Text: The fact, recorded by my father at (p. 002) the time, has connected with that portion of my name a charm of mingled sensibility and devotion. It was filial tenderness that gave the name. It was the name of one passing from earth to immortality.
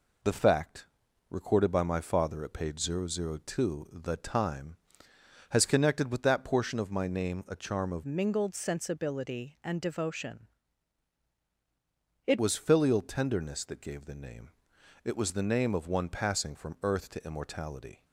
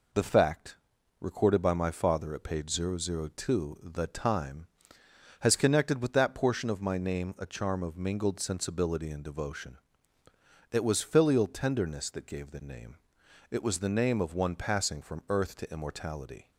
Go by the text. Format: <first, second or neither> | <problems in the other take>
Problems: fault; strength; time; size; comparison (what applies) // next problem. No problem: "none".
second | changes voice from "mingled" to "It"; from 8.0 to 12.3 s; 4.3 s long